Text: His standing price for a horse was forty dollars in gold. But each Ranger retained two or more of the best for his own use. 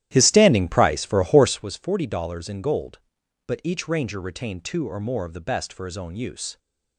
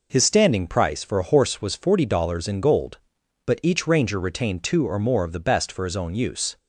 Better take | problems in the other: second | starts louder than the rest; strong; until 1.7 s; 13 dB

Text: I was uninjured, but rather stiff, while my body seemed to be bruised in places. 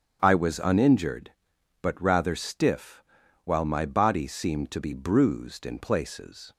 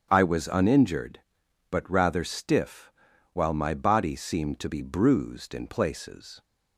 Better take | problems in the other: neither | starts louder than the rest; strong; the same in both

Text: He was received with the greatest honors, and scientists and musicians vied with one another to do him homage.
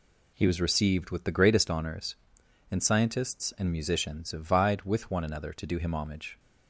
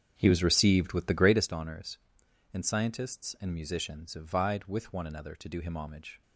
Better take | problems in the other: first | starts louder than the rest; strong; until 1.5 s; 7.5 dB

